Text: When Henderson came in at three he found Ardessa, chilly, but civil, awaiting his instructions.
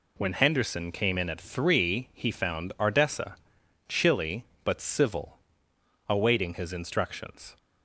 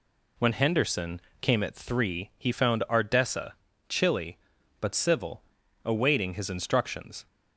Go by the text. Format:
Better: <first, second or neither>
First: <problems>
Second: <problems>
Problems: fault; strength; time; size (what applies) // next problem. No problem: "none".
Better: first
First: none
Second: pauses between "Henderson" and "came"; slight; at 1.1 s; 0.22 s long // skips "in"; at 1.6 s